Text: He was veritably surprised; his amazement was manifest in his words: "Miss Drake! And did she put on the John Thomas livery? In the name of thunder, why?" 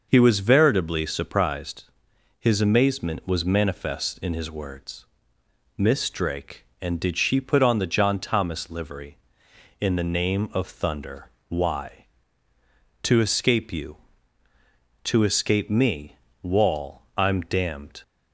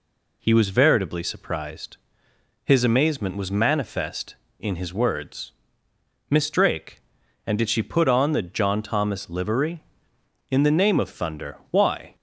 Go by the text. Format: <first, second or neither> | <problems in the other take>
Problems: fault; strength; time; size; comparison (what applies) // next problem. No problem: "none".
second | starts louder than the rest; noticeable; until 1.1 s; 6 dB // goes on to say "To escape you To escape me Wall I'm damned"; strong; from 13.0 s on; 4.9 s long